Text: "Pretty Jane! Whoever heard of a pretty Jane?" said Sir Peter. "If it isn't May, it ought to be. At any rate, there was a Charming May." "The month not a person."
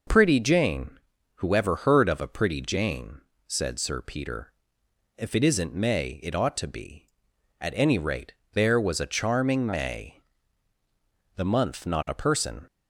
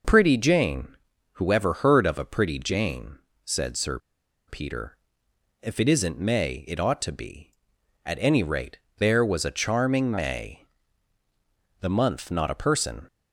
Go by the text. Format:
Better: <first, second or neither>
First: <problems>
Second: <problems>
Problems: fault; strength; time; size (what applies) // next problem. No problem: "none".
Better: first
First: none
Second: pauses between "Sir" and "Peter"; noticeable; at 3.9 s; 0.49 s long